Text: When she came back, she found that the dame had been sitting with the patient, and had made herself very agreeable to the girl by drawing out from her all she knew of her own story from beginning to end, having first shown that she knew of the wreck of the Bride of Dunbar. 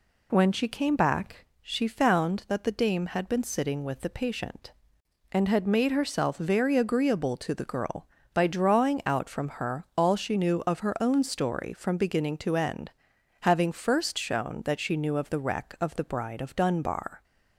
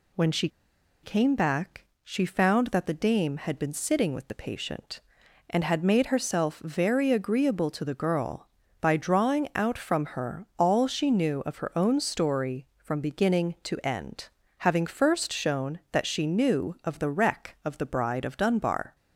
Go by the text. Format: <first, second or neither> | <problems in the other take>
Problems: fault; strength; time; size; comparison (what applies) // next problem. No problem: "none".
first | pauses between "she" and "came"; noticeable; at 0.4 s; 0.54 s long